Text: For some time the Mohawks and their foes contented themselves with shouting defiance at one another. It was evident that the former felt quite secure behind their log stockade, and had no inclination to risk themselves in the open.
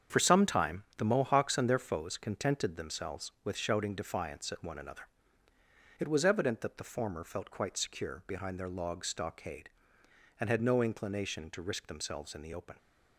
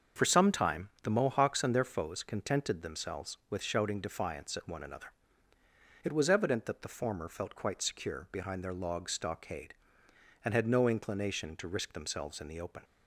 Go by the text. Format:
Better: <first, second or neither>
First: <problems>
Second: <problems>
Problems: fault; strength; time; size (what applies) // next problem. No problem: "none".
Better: second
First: gets quieter; strong; throughout; 8 dB // starts louder than the rest; strong; until 1.2 s; 7.5 dB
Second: starts louder than the rest; until 1.3 s; 6.5 dB